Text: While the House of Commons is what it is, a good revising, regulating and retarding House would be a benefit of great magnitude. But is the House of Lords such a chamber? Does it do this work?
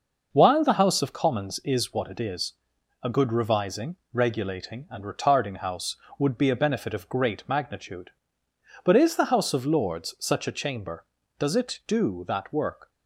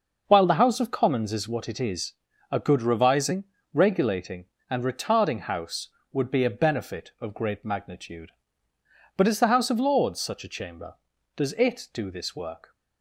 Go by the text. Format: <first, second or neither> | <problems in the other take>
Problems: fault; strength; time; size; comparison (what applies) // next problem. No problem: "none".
second | says "that" for "this"; at 12.2 s